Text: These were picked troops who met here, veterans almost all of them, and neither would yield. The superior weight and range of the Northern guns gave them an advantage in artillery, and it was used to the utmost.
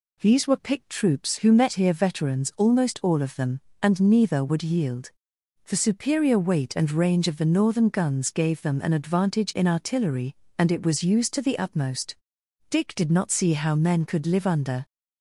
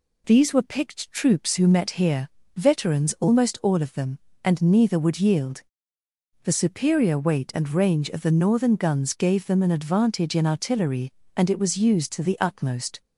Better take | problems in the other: second | goes on to say "Dick did not see how men could live under"; strong; from 12.7 s on; 2.1 s long

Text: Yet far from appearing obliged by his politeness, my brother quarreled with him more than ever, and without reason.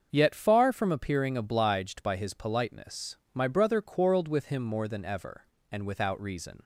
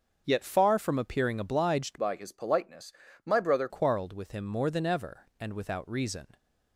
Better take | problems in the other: first | starts louder than the rest; until 1.2 s; 7 dB; also in the first // changes voice from "by" to "brother"; from 1.9 to 3.6 s; 1.7 s long

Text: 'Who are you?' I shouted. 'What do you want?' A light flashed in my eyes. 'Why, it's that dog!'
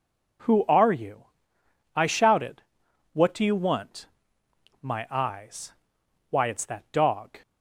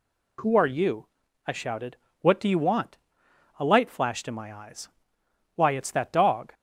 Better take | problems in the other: second | skips "A light flashed in"; at 4.4 s

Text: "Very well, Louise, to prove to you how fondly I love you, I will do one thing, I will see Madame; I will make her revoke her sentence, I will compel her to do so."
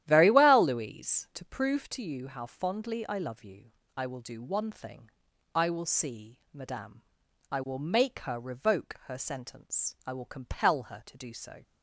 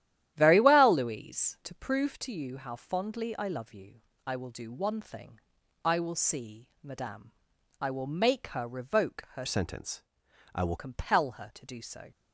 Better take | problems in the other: first | starts louder than the rest; strong; until 1.3 s; 12 dB; strong in the first // changes voice from "sentence" to "will"; from 9.4 to 10.7 s; 1.3 s long

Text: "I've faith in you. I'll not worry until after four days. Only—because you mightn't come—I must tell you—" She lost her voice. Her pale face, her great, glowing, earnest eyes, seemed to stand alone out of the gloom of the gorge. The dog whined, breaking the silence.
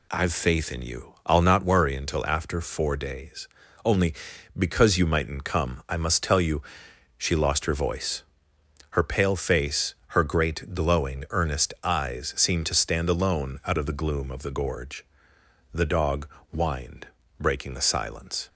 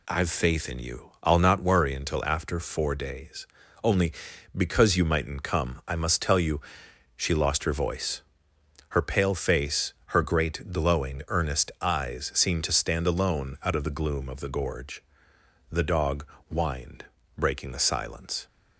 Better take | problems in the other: neither | pauses between "dog" and "whined"; slight; the same in both

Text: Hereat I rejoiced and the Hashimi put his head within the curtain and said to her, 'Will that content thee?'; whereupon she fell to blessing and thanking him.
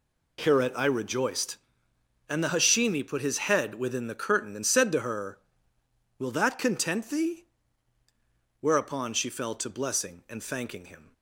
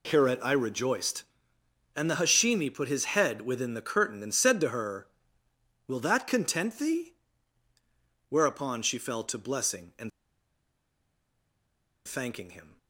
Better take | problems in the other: first | pauses between "and" and "thanking"; strong; at 10.1 s; 1.9 s long

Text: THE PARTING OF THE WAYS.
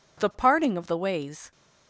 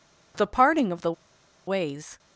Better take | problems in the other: first | pauses between "THE" and "WAYS"; noticeable; at 1.1 s; 0.53 s long

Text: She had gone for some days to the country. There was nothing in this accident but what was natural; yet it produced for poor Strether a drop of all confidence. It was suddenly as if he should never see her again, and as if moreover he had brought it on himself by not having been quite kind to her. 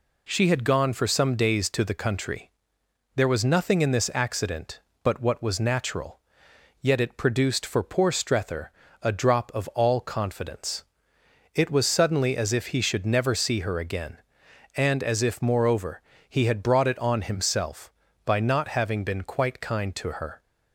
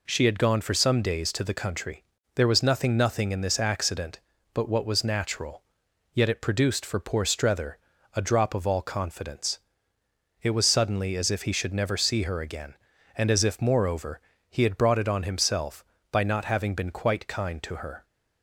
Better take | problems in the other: first | says "nothing" twice; at 2.9 s // pauses between "Strether" and "a"; at 7.7 s; 0.38 s long; slight in the first // pauses between "moreover" and "he"; slight; at 14.2 s; 0.28 s long; slight in the first

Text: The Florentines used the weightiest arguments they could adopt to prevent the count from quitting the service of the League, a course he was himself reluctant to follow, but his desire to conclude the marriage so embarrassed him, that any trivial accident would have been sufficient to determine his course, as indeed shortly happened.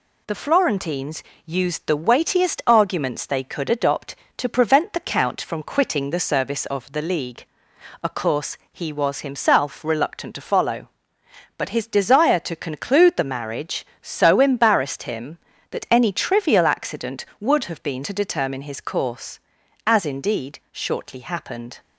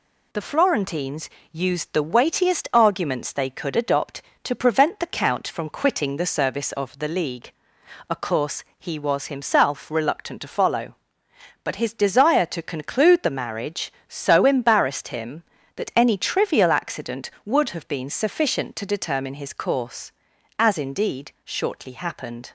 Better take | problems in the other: second | pauses between "Florentines" and "used"; slight; at 1.2 s; 0.22 s long; slight in the second // pauses between "course" and "he"; slight; at 8.5 s; 0.16 s long; slight in the second // skips "sufficient"; at 18.0 s

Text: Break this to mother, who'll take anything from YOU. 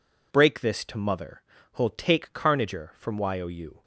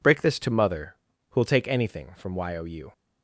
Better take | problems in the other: second | says "carnager" for "anything"; at 2.3 s

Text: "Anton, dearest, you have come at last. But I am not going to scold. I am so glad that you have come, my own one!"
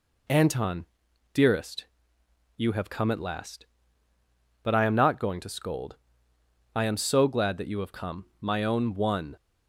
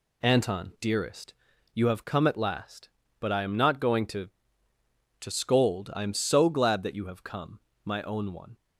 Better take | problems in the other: first | says "to" twice; at 5.1 s

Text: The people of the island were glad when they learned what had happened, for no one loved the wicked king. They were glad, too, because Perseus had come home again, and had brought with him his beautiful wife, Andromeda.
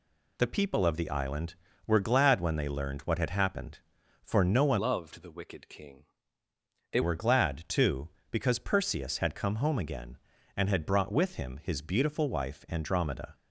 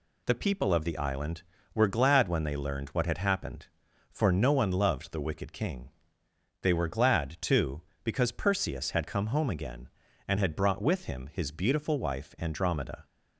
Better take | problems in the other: second | changes voice from "loved" to "They"; from 4.7 to 7.0 s; 2.3 s long

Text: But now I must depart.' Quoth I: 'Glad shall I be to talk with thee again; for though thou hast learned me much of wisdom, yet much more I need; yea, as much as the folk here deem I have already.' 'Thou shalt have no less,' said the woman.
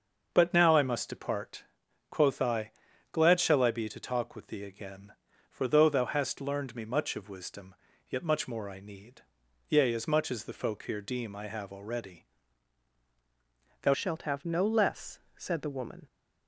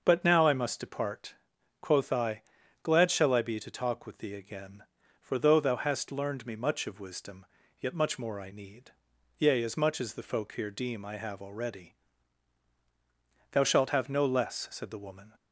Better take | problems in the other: second | starts louder than the rest; until 1.3 s; 6.5 dB; also in the second // changes voice at "shalt"; from 13.9 s on; 2.1 s long

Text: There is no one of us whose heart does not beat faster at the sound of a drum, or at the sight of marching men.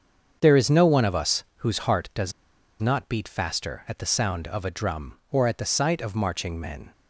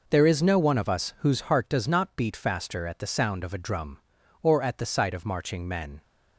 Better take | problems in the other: second | starts louder than the rest; until 1.4 s; 7 dB // pauses between "does" and "not"; noticeable; at 2.3 s; 0.47 s long

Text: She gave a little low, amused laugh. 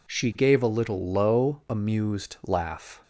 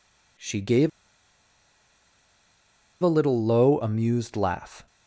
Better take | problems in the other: first | pauses between "gave" and "a"; strong; at 0.8 s; 2.1 s long

